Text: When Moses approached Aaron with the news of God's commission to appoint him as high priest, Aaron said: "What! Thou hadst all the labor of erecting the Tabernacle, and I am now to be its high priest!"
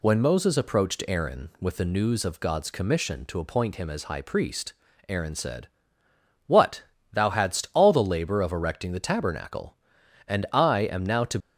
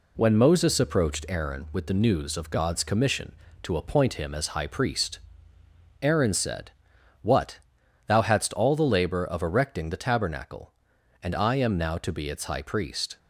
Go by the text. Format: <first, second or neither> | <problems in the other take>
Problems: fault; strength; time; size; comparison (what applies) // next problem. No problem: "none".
second | stops before "be its high priest"; at 11.3 s